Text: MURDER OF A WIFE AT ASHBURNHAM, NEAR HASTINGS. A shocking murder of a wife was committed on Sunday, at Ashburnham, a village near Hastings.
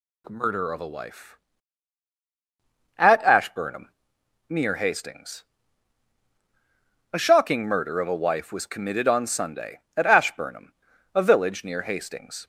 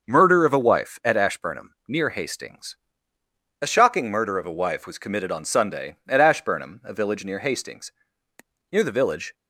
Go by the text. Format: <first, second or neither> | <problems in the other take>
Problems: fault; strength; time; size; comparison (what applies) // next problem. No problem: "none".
first | starts louder than the rest; until 1.1 s; 6.5 dB // goes on to say "Near the village"; noticeable; from 8.6 s on; 0.64 s long